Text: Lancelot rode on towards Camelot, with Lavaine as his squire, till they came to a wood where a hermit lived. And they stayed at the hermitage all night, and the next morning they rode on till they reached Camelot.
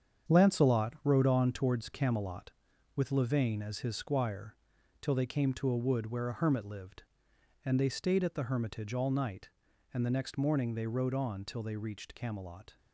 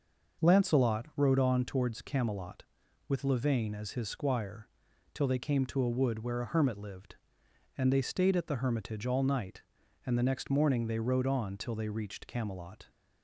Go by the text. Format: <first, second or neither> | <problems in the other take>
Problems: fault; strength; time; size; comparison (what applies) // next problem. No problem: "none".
second | gets quieter; strong; throughout; 8.5 dB // starts louder than the rest; strong; until 1.3 s; 8 dB; noticeable in the second